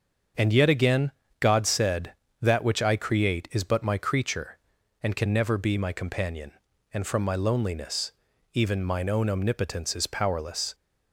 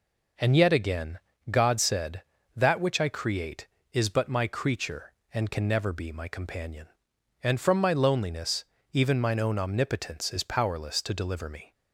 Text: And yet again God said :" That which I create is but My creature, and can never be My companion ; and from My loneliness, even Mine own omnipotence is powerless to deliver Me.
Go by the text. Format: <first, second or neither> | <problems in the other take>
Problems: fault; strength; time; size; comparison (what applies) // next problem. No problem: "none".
second | starts louder than the rest; until 1.6 s; 7 dB // pauses between "again" and "God"; slight; at 1.1 s; 0.28 s long; slight in the second // stops before "to deliver Me"; at 10.7 s